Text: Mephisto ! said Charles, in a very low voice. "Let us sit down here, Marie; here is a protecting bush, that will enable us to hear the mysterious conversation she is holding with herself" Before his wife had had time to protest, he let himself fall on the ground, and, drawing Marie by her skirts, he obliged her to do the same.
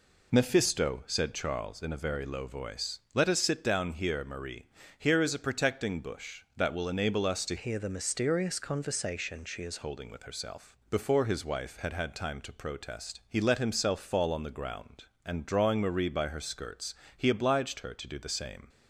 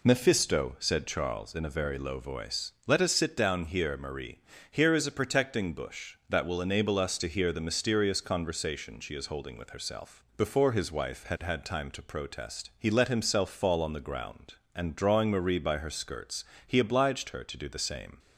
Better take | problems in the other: second | changes voice from "hear" to "is"; from 7.5 to 9.8 s; 2.3 s long

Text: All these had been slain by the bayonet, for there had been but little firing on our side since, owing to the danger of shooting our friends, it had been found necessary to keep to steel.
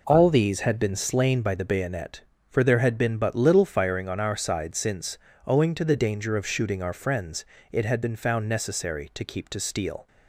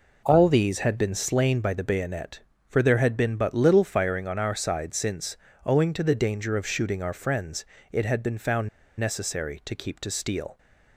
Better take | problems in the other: first | pauses between "found" and "necessary"; slight; at 8.6 s; 0.30 s long

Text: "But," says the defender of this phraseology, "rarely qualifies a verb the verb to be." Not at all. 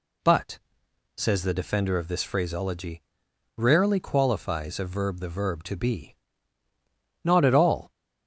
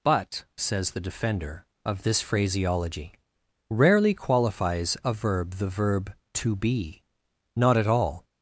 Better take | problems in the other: neither | none

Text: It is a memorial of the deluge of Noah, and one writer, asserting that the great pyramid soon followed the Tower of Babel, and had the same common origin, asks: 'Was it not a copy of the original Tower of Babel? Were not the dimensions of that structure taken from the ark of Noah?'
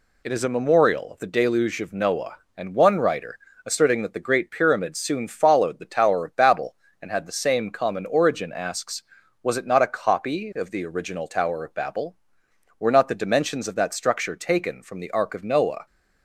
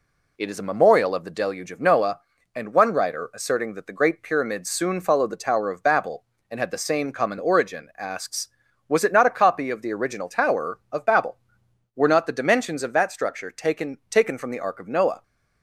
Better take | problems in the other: first | says "taken" twice; at 14.1 s

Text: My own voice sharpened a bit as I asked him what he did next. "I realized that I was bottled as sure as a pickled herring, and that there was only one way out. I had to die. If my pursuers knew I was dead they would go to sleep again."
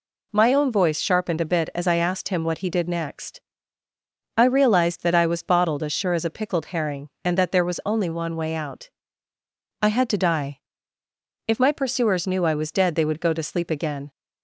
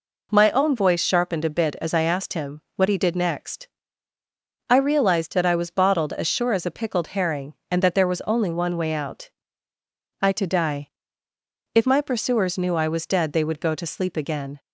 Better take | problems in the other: first | skips "had"; at 10.3 s

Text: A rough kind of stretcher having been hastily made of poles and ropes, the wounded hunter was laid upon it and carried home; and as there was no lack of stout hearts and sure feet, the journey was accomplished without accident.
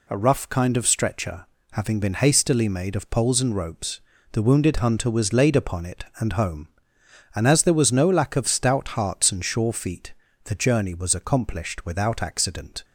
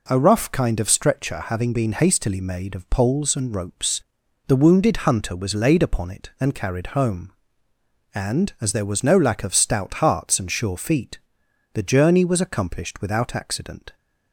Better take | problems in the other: second | pauses between "stretcher" and "having"; slight; at 1.4 s; 0.28 s long // skips "carried"; at 6.3 s

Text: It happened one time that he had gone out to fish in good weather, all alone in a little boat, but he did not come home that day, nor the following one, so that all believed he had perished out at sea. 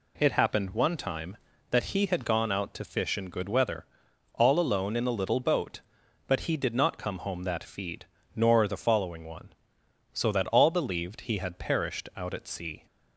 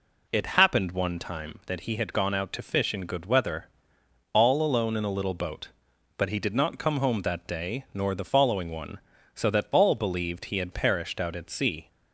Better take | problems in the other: second | says "feed" for "day"; at 7.6 s

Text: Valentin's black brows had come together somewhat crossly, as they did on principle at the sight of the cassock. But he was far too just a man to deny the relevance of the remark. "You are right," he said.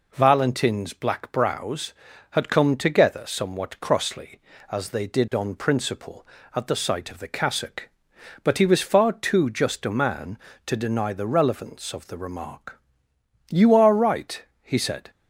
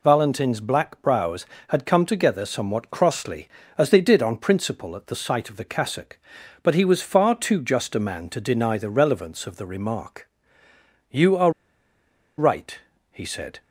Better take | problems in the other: first | pauses between "are" and "right"; noticeable; at 11.5 s; 0.86 s long

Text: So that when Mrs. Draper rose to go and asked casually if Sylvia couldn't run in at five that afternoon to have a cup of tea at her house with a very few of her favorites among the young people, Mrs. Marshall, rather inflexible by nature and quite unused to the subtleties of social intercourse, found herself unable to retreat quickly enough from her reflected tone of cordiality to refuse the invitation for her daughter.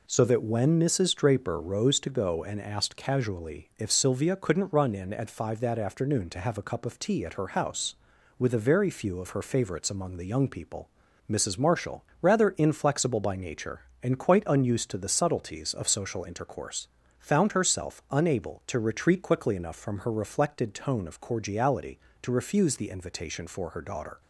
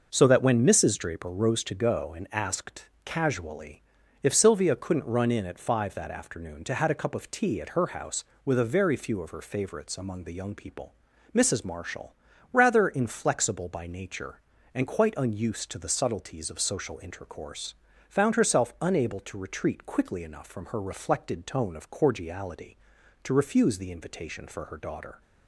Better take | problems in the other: first | pauses between "asked" and "casually"; slight; at 2.8 s; 0.16 s long // pauses between "casually" and "if"; at 3.8 s; 0.44 s long // says "had" for "have"; at 6.7 s

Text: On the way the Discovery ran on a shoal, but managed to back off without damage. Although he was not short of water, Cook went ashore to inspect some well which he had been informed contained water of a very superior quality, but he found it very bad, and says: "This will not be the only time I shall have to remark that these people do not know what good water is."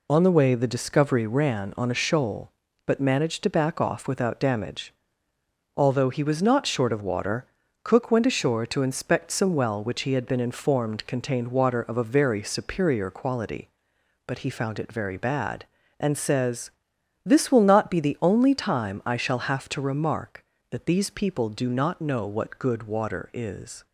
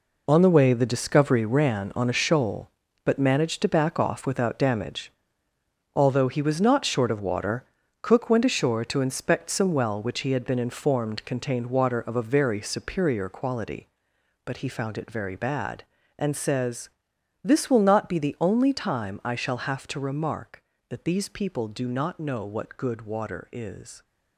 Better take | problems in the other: first | gets quieter; strong; throughout; 10.5 dB

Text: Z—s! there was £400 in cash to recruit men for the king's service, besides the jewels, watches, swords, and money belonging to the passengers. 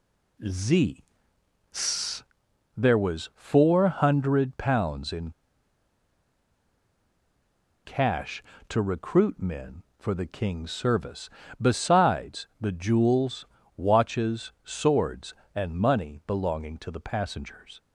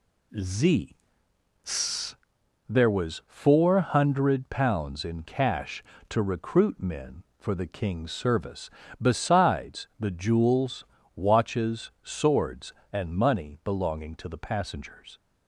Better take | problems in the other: second | pauses between "in" and "cash"; strong; at 5.3 s; 2.5 s long

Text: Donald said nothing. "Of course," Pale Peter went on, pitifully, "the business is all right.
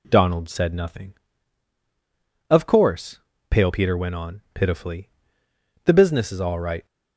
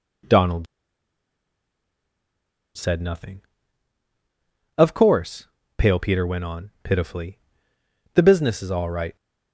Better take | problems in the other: first | pauses between "Donald" and "said"; strong; at 0.6 s; 2.0 s long

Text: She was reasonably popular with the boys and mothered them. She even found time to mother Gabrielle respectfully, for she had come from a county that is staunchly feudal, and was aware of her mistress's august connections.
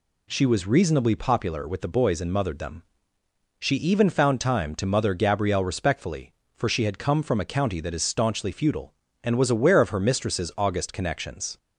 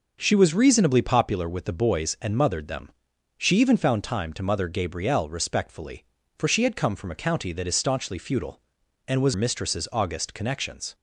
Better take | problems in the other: first | skips "aware of her"; at 9.3 s

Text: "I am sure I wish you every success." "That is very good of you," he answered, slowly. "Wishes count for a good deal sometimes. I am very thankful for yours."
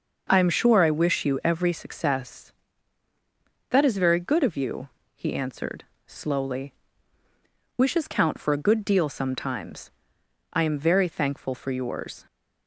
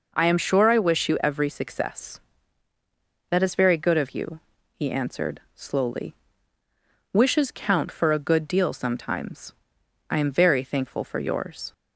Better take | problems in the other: neither | none

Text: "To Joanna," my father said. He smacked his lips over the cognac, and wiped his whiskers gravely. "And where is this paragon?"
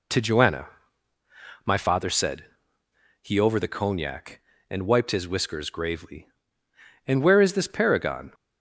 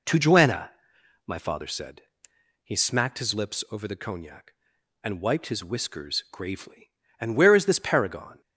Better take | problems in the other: second | skips "smacked his lips"; at 3.3 s

